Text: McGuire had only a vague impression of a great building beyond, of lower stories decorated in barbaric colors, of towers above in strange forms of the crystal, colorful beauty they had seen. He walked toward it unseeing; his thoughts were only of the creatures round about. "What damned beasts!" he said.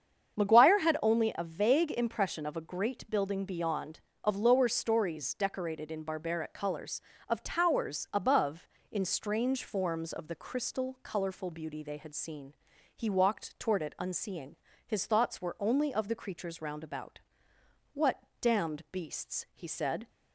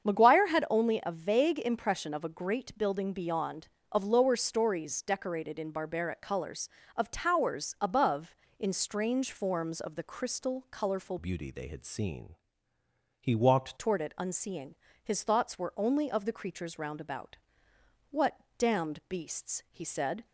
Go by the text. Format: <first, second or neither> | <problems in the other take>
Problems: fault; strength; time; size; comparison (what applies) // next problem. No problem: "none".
first | starts louder than the rest; strong; until 1.1 s; 7.5 dB; strong in the first // changes voice from "beauty" to "walked"; from 11.1 to 13.7 s; 2.6 s long // pauses between "What" and "damned"; slight; at 18.3 s; 0.22 s long; slight in the first